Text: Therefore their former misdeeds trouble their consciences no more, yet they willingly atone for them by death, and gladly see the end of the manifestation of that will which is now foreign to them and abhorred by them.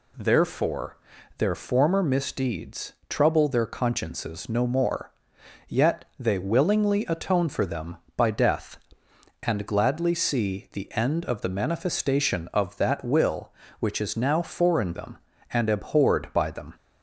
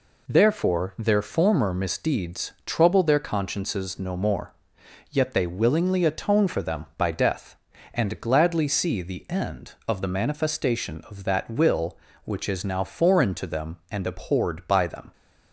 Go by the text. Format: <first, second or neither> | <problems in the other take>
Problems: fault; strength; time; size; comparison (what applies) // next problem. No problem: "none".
second | pauses between "Therefore" and "their"; at 0.9 s; 0.40 s long // pauses between "misdeeds" and "trouble"; slight; at 2.9 s; 0.16 s long // skips "to"; at 14.9 s